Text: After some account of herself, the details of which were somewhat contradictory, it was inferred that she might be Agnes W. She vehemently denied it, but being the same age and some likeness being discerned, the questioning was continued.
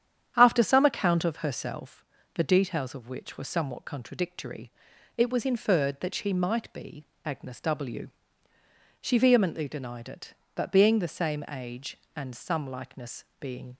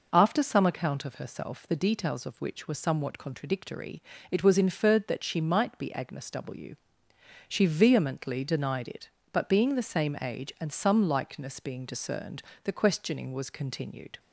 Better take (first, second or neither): second